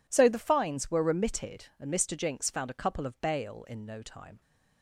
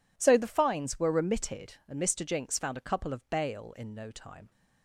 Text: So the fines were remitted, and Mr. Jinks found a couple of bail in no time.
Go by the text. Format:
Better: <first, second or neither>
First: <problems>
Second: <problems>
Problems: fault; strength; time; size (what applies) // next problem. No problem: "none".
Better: neither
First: none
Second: none